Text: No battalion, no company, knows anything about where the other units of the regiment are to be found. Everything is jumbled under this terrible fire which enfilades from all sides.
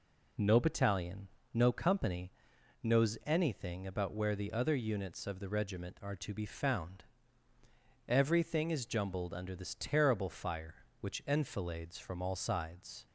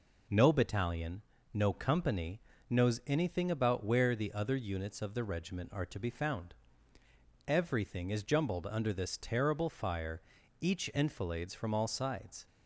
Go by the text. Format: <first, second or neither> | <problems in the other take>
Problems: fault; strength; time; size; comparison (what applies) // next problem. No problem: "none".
first | says "each" for "which"; at 10.5 s